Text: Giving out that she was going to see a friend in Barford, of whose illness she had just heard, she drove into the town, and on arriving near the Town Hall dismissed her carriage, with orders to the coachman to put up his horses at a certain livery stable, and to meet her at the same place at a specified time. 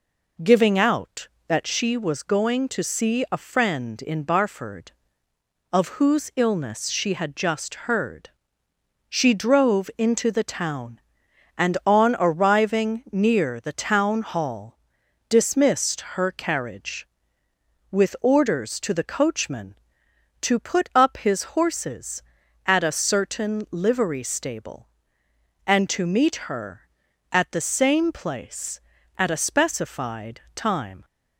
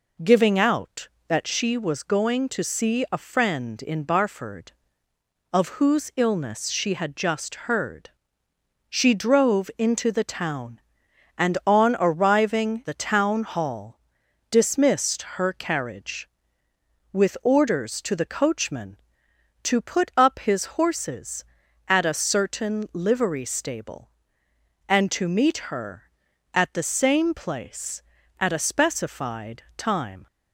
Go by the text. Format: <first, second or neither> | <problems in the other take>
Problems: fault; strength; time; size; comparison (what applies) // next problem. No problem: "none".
first | skips "near"; at 12.8 s // pauses between "Hall" and "dismissed"; noticeable; at 13.9 s; 0.52 s long; noticeable in the first // pauses between "specified" and "time"; slight; at 29.6 s; 0.16 s long; slight in the first